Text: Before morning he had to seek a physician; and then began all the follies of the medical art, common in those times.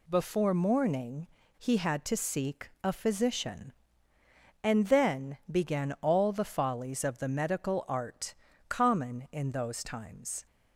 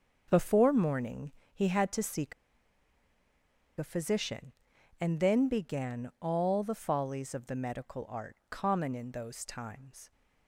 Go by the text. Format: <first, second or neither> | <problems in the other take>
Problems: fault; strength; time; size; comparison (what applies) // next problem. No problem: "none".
first | starts louder than the rest; until 1.2 s; 6.5 dB // pauses between "morning" and "he"; slight; at 1.3 s; 0.24 s long; slight in the first // pauses between "seek" and "a"; strong; at 2.3 s; 1.4 s long